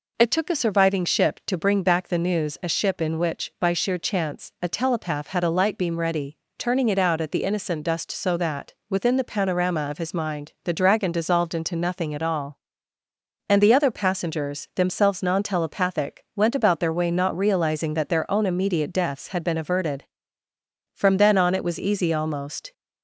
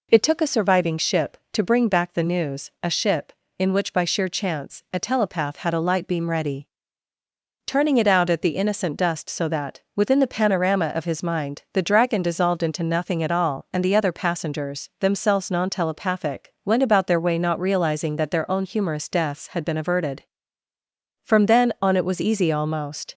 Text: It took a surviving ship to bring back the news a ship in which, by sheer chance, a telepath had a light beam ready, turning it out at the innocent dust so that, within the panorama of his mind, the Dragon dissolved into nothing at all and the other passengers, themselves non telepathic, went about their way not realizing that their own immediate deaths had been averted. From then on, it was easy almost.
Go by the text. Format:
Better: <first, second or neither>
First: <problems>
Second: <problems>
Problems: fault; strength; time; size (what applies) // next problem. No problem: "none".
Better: first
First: none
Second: says "humorous" for "immediate"; at 18.6 s